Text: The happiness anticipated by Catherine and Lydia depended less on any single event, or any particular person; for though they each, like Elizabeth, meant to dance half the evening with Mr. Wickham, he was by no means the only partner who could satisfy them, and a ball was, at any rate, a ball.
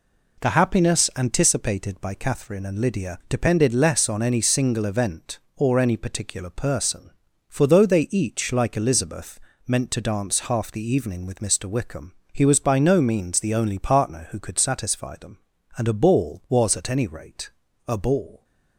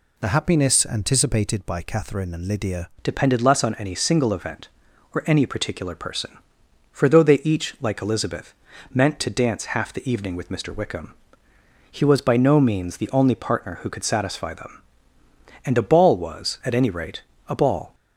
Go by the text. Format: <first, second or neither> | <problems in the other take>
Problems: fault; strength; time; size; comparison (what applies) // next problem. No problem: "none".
first | changes voice at "depended"; from 3.0 s on; 14.9 s long